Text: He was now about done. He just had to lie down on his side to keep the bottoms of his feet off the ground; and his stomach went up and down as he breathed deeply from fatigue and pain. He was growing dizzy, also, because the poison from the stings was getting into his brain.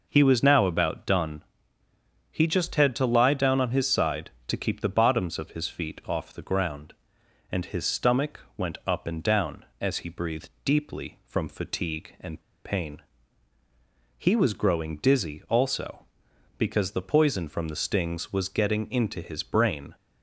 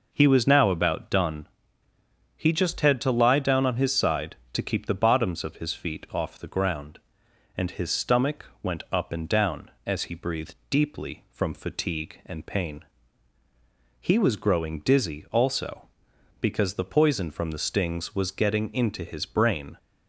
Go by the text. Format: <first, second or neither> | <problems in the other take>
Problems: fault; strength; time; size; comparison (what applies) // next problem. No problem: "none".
second | pauses between "stomach" and "went"; slight; at 8.4 s; 0.16 s long; slight in the second // pauses between "breathed" and "deeply"; slight; at 10.4 s; 0.16 s long; slight in the second // pauses between "and" and "pain"; slight; at 12.4 s; 0.24 s long